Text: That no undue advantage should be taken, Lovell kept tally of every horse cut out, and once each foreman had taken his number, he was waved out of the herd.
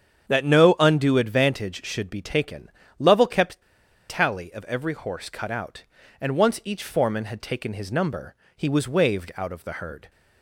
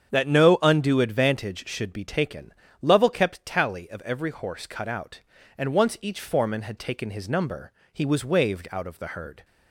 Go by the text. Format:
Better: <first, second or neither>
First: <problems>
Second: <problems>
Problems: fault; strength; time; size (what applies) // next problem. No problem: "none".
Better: second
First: starts louder than the rest; strong; until 1.3 s; 8 dB // pauses between "kept" and "tally"; noticeable; at 3.6 s; 0.46 s long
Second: starts louder than the rest; strong; until 1.1 s; 8 dB